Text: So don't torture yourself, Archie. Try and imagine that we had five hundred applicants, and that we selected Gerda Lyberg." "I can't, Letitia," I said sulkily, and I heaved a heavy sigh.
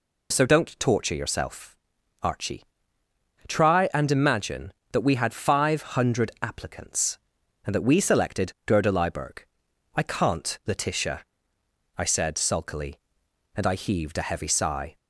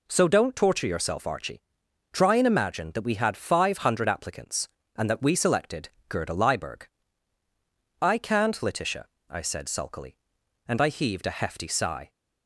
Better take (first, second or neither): first